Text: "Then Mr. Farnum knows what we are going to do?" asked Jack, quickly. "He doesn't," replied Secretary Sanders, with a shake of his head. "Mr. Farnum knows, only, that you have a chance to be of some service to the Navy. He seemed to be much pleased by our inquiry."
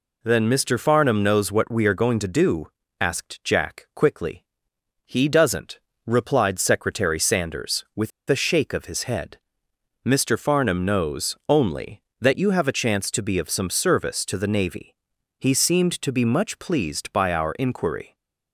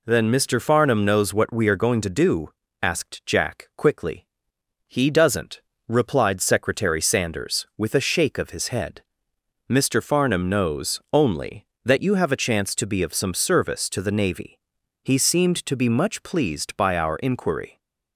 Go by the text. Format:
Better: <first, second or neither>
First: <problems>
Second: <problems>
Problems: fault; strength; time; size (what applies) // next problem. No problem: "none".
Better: second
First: pauses between "with" and "a"; slight; at 8.1 s; 0.19 s long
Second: none